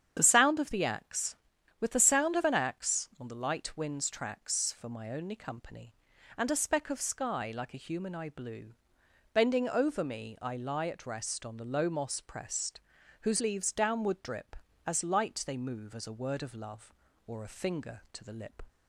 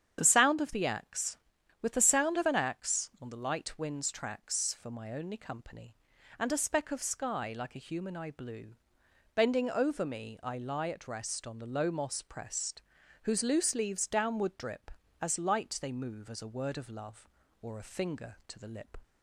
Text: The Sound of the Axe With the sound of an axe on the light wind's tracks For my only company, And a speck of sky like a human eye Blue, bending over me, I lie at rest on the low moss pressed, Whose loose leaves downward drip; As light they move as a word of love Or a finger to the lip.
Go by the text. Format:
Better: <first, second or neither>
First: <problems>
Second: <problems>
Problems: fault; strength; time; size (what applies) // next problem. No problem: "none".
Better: second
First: starts louder than the rest; strong; until 1.1 s; 8.5 dB // skips "loose"; at 13.4 s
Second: starts louder than the rest; strong; until 1.2 s; 8.5 dB